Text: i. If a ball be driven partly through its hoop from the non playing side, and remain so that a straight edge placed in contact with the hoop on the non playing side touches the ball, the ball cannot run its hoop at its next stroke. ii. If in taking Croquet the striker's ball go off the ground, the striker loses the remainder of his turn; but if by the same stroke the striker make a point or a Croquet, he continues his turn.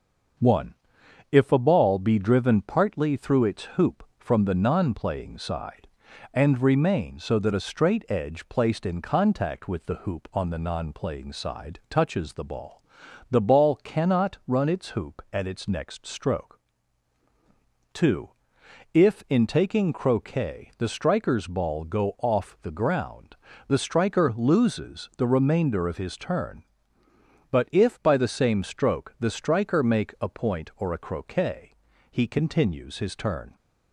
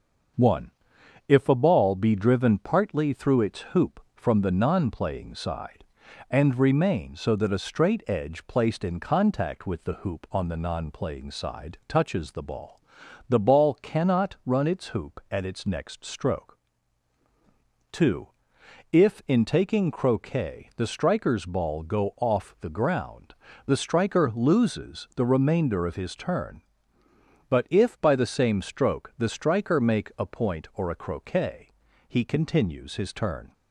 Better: neither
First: starts louder than the rest; until 1.9 s; 6.5 dB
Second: starts louder than the rest; until 1.9 s; 6.5 dB

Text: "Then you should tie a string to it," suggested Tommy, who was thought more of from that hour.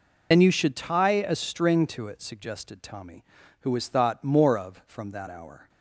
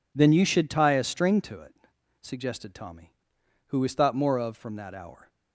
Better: second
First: loses the start of "Then"; at 0.3 s; 85 ms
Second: none

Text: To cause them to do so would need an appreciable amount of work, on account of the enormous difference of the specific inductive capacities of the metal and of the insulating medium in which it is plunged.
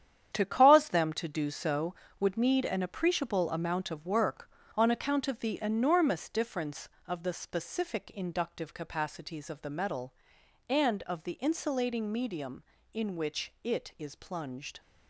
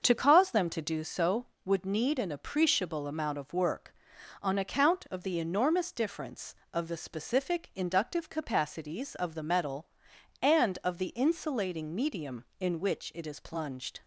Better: second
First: gets quieter; strong; throughout; 9 dB // starts louder than the rest; strong; until 1.3 s; 9.5 dB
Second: starts louder than the rest; until 1.0 s; 6.5 dB

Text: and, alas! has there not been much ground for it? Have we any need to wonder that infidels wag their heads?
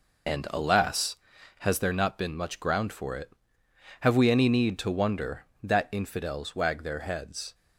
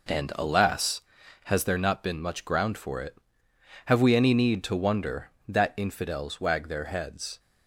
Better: second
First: loses the start of "and"; at 0.2 s; 55 ms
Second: none

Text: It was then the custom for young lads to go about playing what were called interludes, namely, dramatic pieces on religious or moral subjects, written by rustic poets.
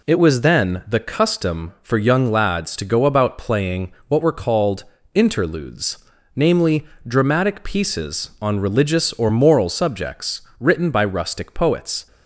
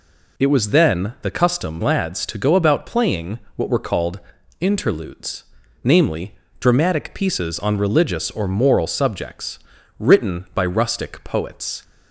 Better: first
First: pauses between "playing" and "what"; slight; at 3.9 s; 0.16 s long // pauses between "called" and "interludes"; slight; at 4.8 s; 0.32 s long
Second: skips "for young"; at 1.8 s // pauses between "playing" and "what"; slight; at 3.3 s; 0.18 s long // pauses between "called" and "interludes"; at 4.2 s; 0.40 s long

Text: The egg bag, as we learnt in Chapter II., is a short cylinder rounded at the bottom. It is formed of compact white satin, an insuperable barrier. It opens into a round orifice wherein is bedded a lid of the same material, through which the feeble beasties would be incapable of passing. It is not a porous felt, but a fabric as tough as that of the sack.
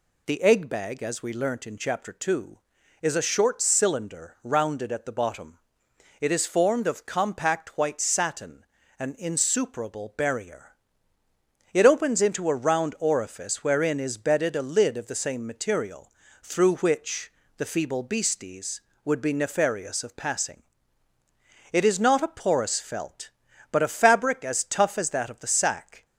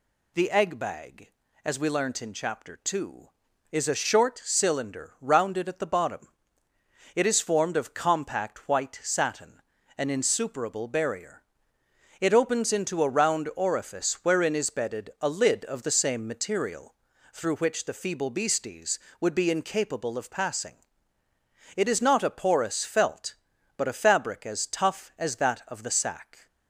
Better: second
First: pauses between "which" and "the"; slight; at 17.3 s; 0.26 s long // says "nefarious" for "incapable"; at 19.3 s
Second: none

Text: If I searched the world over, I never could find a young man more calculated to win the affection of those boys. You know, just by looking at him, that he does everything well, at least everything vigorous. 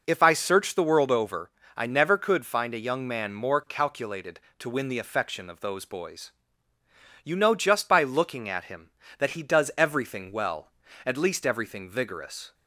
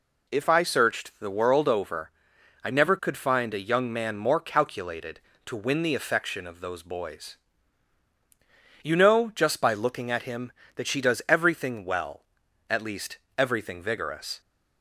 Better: first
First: none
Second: says "she" for "he"; at 10.8 s // pauses between "least" and "everything"; slight; at 13.1 s; 0.20 s long

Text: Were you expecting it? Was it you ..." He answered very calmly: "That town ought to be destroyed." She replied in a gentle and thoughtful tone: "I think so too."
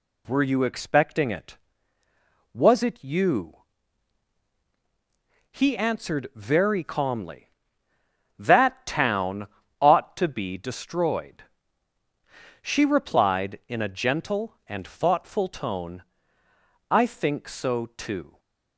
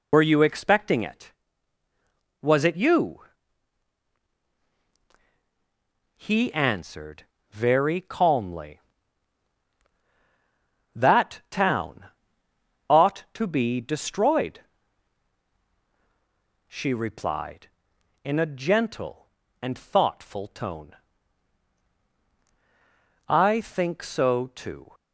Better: first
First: pauses between "town" and "ought"; slight; at 9.4 s; 0.32 s long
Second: loses the start of "Were"; at 0.1 s; 85 ms // pauses between "answered" and "very"; slight; at 7.2 s; 0.28 s long // pauses between "town" and "ought"; noticeable; at 12.0 s; 0.82 s long

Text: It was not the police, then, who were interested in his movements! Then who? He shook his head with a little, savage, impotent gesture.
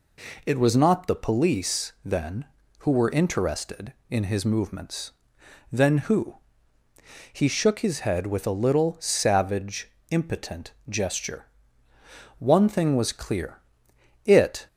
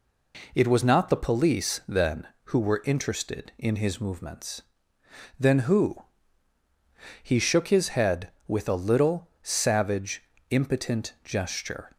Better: second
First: pauses between "impotent" and "gesture"; slight; at 10.7 s; 0.16 s long // goes on to say "One thing was clear it"; strong; from 12.3 s on; 2.2 s long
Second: none

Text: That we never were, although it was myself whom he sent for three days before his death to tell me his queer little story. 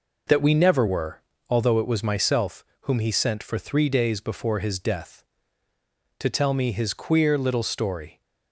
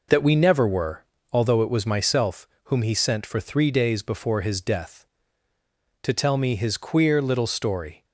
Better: neither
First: pauses between "myself" and "whom"; slight; at 2.6 s; 0.18 s long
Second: pauses between "myself" and "whom"; slight; at 2.4 s; 0.18 s long

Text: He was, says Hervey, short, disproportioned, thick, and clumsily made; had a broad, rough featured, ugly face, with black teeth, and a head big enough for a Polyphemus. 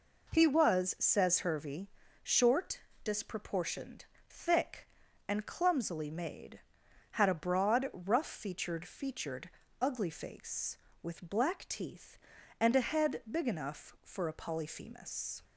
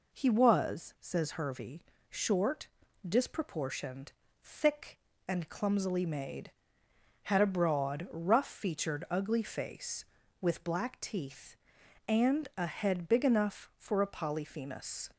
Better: second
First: says "featured" twice; at 8.8 s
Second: none

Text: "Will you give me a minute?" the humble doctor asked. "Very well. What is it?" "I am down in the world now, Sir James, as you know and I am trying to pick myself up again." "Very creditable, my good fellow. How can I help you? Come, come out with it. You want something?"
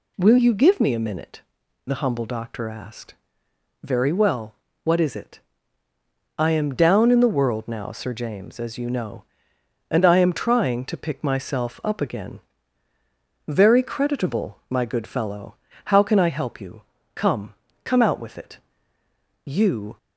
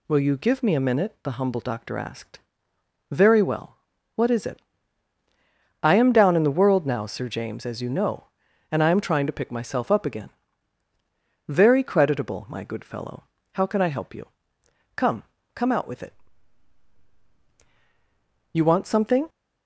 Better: second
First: stops before "want something"; at 19.9 s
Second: none

